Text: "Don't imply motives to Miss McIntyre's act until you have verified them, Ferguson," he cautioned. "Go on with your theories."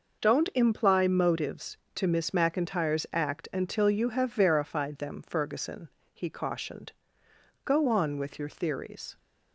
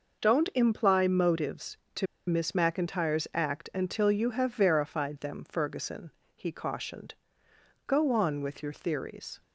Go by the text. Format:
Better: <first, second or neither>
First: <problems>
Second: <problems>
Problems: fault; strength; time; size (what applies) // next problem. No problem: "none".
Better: first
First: none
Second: pauses between "to" and "Miss"; slight; at 2.0 s; 0.23 s long